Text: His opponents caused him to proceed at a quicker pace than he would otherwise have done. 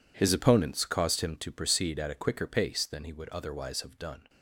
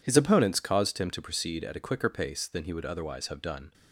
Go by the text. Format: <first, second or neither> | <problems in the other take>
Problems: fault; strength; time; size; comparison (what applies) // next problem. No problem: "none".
second | gets quieter; strong; throughout; 17 dB